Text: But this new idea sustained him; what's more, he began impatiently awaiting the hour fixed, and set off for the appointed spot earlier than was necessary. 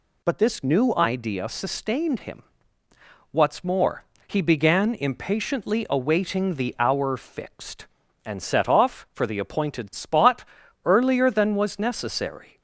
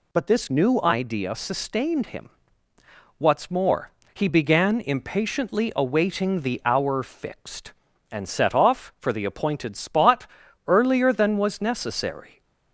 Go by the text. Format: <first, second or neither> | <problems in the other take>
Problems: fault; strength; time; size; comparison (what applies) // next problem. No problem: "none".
neither | pauses between "spot" and "earlier"; the same in both